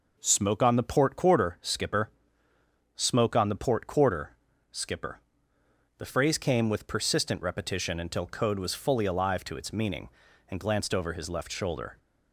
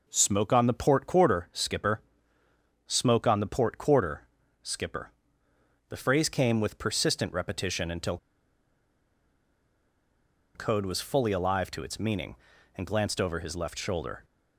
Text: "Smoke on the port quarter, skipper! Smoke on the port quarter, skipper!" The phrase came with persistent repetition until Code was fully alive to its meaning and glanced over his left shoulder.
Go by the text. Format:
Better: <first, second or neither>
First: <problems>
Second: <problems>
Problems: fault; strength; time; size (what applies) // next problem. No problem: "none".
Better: first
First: none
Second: pauses between "until" and "Code"; strong; at 8.1 s; 2.3 s long